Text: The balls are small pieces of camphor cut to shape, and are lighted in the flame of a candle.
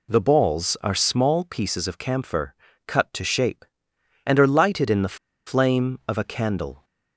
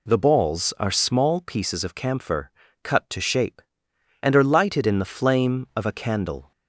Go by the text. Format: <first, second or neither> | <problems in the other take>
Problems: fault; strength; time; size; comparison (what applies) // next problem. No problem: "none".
second | pauses between "camphor" and "cut"; slight; at 2.5 s; 0.32 s long; slight in the second // pauses between "the" and "flame"; slight; at 5.1 s; 0.31 s long